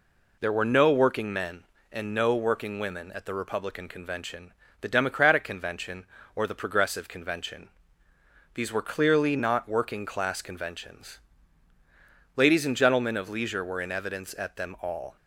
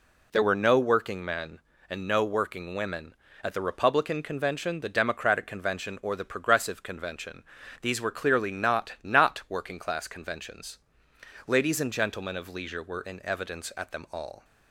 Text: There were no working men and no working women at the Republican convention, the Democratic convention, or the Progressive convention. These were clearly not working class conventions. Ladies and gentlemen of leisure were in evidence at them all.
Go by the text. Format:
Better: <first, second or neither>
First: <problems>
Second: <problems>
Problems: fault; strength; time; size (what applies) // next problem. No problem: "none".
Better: first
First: none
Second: says "not" twice; at 9.0 s